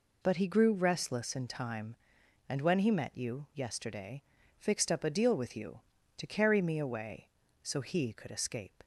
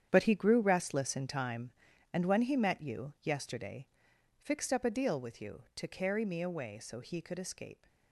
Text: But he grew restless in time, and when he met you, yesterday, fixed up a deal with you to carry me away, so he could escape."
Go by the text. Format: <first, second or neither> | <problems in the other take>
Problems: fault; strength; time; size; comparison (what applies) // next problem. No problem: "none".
first | gets quieter; strong; throughout; 12.5 dB